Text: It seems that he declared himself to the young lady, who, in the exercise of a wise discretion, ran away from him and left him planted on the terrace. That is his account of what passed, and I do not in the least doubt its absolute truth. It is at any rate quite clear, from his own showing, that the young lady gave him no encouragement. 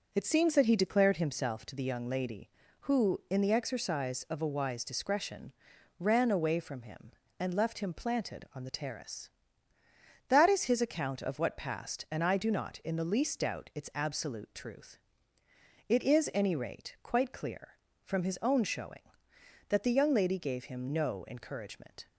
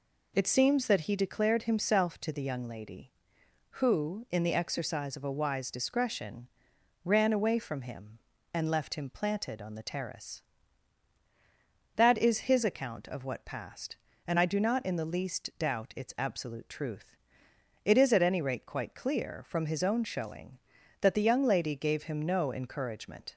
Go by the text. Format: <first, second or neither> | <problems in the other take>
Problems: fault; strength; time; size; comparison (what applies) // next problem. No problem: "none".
second | skips "at"; at 16.3 s